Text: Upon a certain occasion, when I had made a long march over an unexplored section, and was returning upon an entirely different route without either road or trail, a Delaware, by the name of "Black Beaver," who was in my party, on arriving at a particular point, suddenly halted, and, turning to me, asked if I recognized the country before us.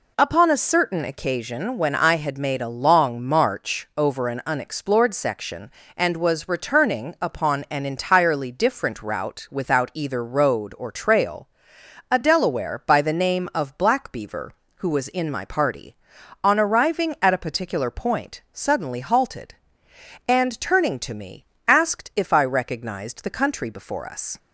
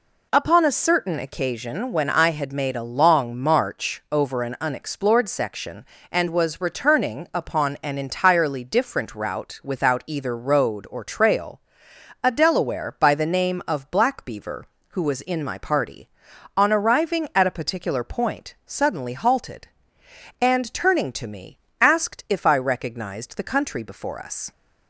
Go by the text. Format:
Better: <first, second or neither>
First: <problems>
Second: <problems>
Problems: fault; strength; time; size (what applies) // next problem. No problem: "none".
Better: neither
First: none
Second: none